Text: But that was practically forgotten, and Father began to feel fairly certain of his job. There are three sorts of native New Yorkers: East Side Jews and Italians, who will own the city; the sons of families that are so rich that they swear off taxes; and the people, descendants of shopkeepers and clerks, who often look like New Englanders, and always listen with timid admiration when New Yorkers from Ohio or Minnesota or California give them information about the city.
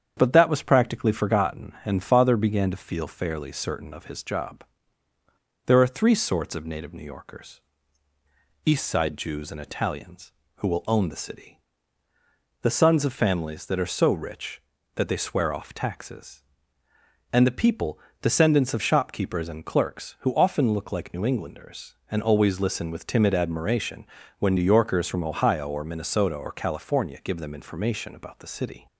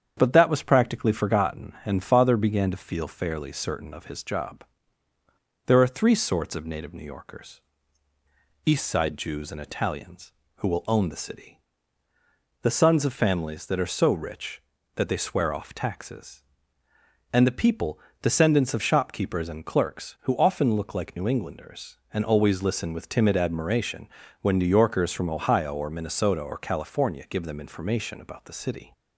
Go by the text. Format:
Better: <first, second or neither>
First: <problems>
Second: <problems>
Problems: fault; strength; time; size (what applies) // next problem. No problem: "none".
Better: neither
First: starts louder than the rest; strong; until 1.1 s; 8 dB // pauses between "admiration" and "when"; slight; at 24.0 s; 0.36 s long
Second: starts louder than the rest; strong; until 1.1 s; 8 dB // pauses between "admiration" and "when"; slight; at 24.0 s; 0.36 s long